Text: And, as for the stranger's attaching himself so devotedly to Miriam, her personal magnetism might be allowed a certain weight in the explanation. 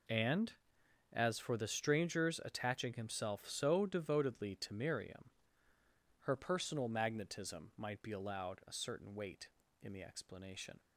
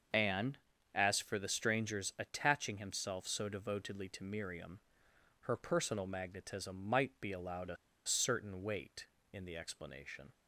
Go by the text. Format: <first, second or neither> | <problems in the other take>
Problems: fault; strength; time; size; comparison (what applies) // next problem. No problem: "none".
first | starts louder than the rest; until 1.4 s; 6.5 dB // pauses between "a" and "certain"; slight; at 7.7 s; 0.29 s long